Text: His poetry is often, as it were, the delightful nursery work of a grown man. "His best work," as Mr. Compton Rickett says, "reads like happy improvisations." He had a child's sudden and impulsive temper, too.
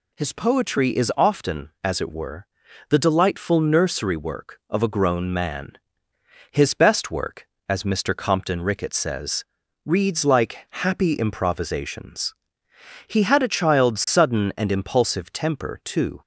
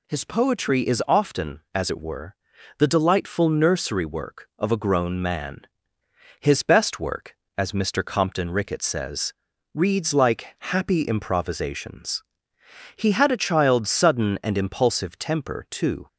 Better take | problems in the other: neither | none

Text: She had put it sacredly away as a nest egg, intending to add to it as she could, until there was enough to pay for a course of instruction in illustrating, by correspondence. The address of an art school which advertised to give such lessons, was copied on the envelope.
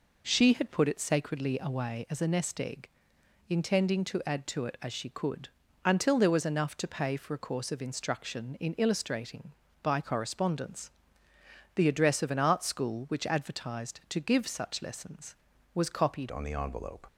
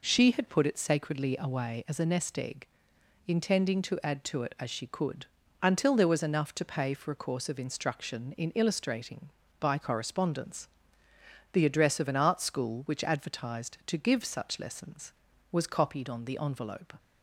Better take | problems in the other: second | changes voice at "on"; from 16.2 s on; 0.8 s long

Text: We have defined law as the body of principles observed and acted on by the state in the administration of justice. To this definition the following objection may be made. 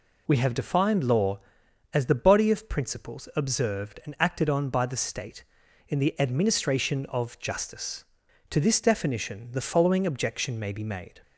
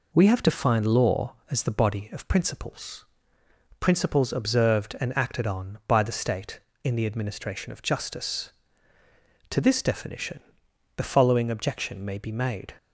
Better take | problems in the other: first | says "principles" twice; at 3.7 s // pauses between "definition" and "the"; noticeable; at 10.3 s; 0.58 s long

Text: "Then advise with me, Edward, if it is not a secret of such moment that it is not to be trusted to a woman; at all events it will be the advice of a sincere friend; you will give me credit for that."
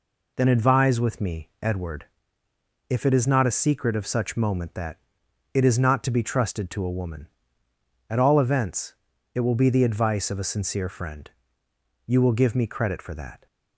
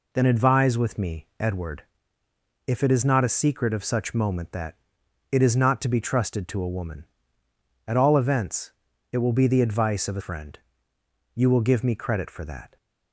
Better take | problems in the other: first | pauses between "that" and "it"; noticeable; at 4.7 s; 0.56 s long; noticeable in the first // pauses between "events" and "it"; at 8.7 s; 0.40 s long; also in the first // skips "sincere"; at 10.2 s

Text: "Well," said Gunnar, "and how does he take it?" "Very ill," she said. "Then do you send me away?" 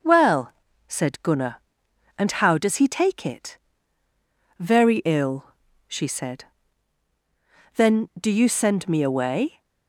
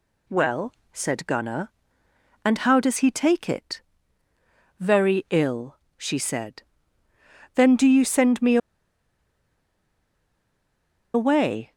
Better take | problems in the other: first | pauses between "me" and "away"; strong; at 8.5 s; 2.5 s long

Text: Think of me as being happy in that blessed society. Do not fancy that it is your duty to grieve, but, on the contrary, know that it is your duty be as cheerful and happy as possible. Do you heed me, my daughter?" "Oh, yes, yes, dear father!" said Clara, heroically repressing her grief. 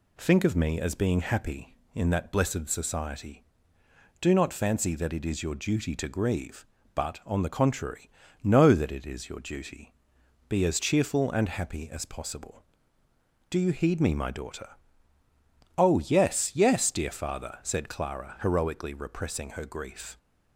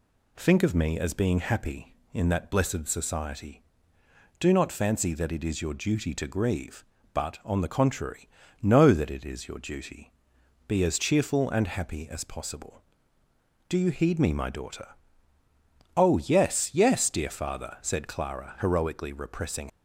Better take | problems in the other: first | pauses between "duty" and "be"; noticeable; at 10.1 s; 0.56 s long; noticeable in the first // stops before "her grief"; at 19.6 s

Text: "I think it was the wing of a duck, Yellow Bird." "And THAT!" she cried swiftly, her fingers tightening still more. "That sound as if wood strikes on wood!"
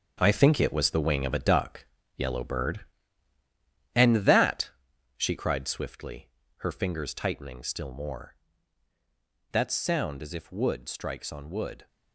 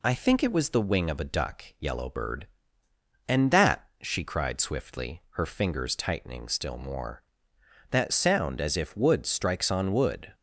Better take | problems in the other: second | gets quieter; strong; throughout; 9.5 dB

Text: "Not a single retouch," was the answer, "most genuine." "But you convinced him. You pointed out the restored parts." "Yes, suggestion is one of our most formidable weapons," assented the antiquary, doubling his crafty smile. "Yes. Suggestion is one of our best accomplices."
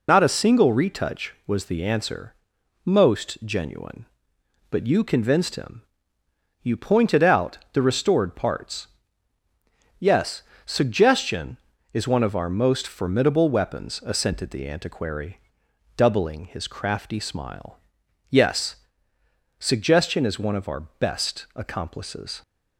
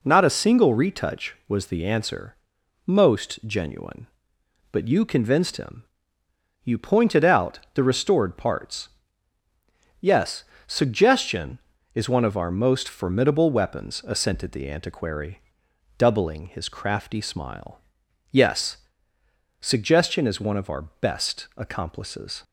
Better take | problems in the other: second | loses the start of "Not"; at 0.0 s; 70 ms // pauses between "out" and "the"; slight; at 7.5 s; 0.16 s long; slight in the second

